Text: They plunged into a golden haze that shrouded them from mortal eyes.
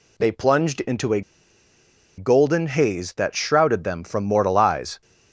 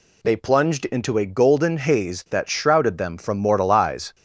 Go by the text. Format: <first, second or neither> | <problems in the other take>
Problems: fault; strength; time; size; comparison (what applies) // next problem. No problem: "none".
second | pauses between "a" and "golden"; noticeable; at 1.2 s; 0.96 s long